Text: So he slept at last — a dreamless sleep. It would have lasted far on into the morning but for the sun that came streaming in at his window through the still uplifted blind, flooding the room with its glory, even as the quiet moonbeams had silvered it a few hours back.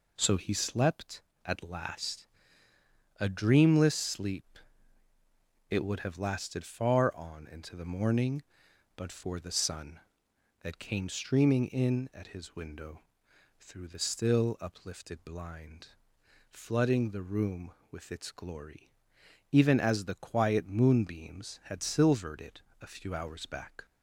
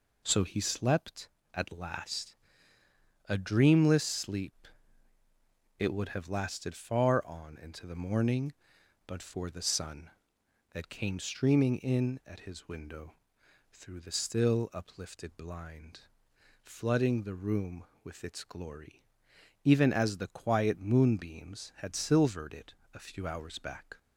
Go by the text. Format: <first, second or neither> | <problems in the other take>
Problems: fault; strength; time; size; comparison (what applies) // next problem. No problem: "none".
neither | pauses between "window" and "through"; noticeable; the same in both // pauses between "it" and "a"; slight; the same in both